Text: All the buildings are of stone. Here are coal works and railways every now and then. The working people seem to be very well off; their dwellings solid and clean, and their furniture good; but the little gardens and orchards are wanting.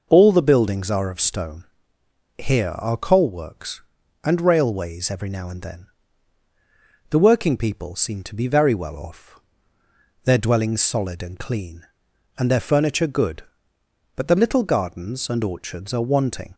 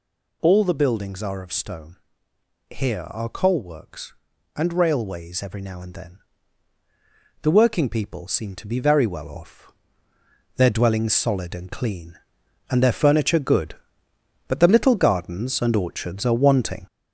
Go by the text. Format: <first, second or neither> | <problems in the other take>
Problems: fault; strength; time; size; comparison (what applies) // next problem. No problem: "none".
first | gets louder; noticeable; throughout; 4.5 dB